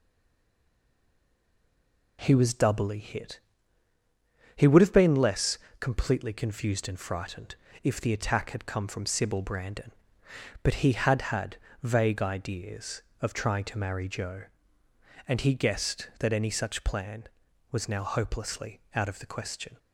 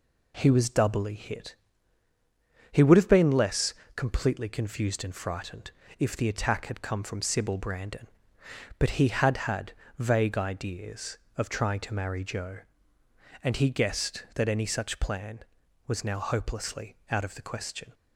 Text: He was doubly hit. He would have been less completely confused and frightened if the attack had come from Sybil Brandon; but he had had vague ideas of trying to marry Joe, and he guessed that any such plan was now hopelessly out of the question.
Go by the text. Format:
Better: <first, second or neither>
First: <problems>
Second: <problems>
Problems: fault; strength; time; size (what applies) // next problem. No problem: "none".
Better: second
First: stays silent before the first word; until 2.1 s; 2.1 s long // pauses between "less" and "completely"; slight; at 5.5 s; 0.22 s long // pauses between "frightened" and "if"; slight; at 7.5 s; 0.26 s long // pauses between "had" and "vague"; slight; at 11.5 s; 0.26 s long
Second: pauses between "less" and "completely"; slight; at 3.7 s; 0.22 s long // pauses between "frightened" and "if"; slight; at 5.7 s; 0.26 s long // pauses between "had" and "vague"; slight; at 9.7 s; 0.26 s long